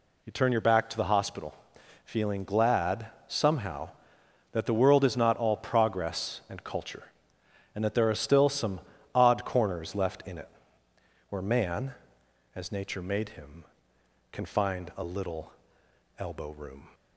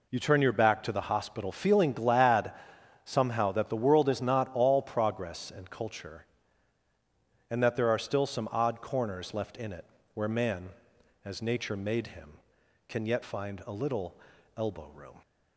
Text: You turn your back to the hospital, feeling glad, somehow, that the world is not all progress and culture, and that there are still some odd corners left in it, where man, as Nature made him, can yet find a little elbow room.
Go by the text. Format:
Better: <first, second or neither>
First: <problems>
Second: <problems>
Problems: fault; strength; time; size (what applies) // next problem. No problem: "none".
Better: second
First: pauses between "some" and "odd"; slight; at 8.7 s; 0.36 s long // skips "yet"; at 14.4 s // pauses between "little" and "elbow"; noticeable; at 15.5 s; 0.66 s long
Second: pauses between "little" and "elbow"; at 14.1 s; 0.40 s long